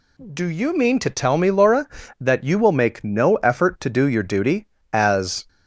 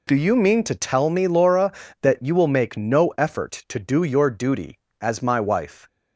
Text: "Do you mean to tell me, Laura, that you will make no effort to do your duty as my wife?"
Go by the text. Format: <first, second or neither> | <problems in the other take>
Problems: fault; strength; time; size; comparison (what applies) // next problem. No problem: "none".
second | stops before "my wife"; at 5.4 s